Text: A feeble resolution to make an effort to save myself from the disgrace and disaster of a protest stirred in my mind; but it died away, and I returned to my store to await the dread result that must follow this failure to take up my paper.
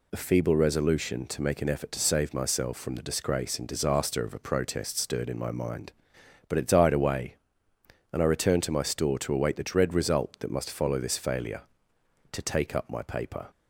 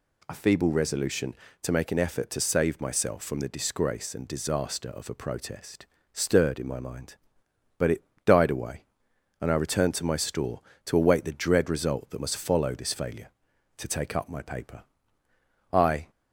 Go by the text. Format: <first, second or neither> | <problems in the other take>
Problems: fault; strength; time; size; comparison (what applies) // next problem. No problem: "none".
first | pauses between "protest" and "stirred"; slight; at 5.8 s; 0.28 s long // pauses between "it" and "died"; slight; at 8.0 s; 0.20 s long // goes on to say "I"; slight; from 15.7 s on; 0.38 s long